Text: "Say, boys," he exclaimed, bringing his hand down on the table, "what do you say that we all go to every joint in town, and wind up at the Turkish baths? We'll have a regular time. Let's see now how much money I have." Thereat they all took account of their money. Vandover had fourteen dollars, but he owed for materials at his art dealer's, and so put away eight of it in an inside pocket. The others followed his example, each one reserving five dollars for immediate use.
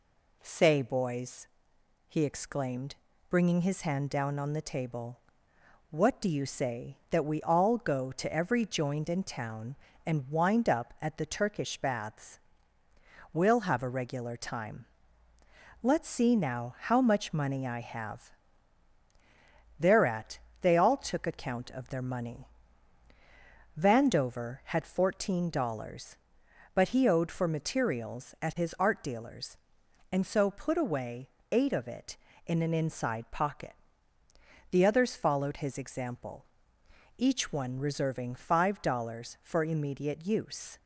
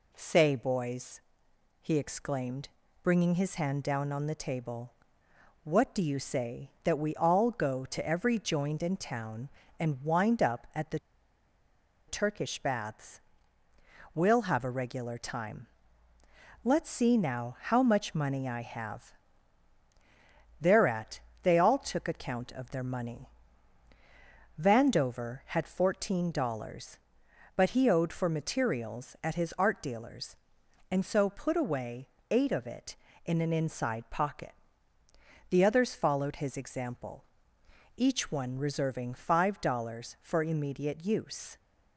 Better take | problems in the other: first | pauses between "the" and "Turkish"; at 10.9 s; 1.0 s long // pauses between "Thereat" and "they"; slight; at 21.2 s; 0.22 s long; slight in the first // pauses between "away" and "eight"; slight; at 32.0 s; 0.22 s long; slight in the first

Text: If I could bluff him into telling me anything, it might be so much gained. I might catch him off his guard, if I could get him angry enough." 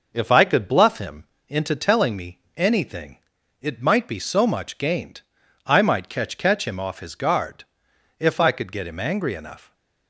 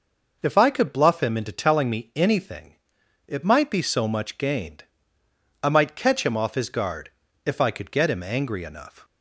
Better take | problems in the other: second | pauses between "him" and "into"; slight; at 1.2 s; 0.24 s long // pauses between "me" and "anything"; slight; at 2.3 s; 0.16 s long // says "catch" twice; at 6.3 s

